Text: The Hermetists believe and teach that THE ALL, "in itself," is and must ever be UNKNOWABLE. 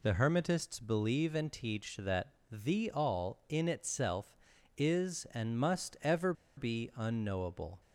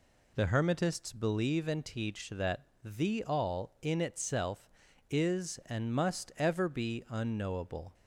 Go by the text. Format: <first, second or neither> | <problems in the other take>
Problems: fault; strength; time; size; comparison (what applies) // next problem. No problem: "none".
second | pauses between "that" and "THE"; slight; at 2.3 s; 0.18 s long; slight in the second // pauses between "ever" and "be"; slight; at 6.3 s; 0.24 s long